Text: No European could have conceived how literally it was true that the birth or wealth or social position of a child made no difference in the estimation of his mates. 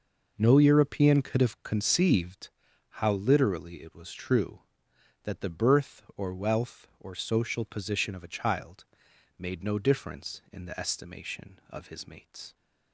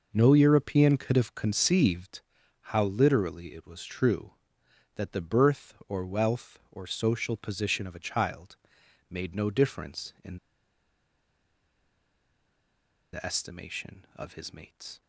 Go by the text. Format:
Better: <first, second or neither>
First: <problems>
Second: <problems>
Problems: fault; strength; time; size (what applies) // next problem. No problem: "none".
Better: first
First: pauses between "conceived" and "how"; at 2.5 s; 0.40 s long // pauses between "child" and "made"; noticeable; at 8.8 s; 0.54 s long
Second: pauses between "conceived" and "how"; at 2.2 s; 0.40 s long // pauses between "child" and "made"; noticeable; at 8.5 s; 0.54 s long // pauses between "in" and "the"; strong; at 10.3 s; 2.7 s long